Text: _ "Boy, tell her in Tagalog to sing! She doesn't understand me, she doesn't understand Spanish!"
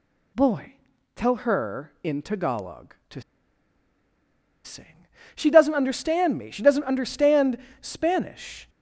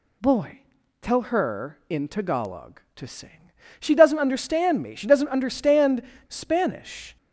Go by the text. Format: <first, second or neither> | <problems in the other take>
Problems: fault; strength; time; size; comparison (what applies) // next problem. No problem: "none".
second | pauses between "to" and "sing"; strong; at 3.2 s; 1.4 s long // pauses between "understand" and "Spanish"; slight; at 7.5 s; 0.24 s long; slight in the second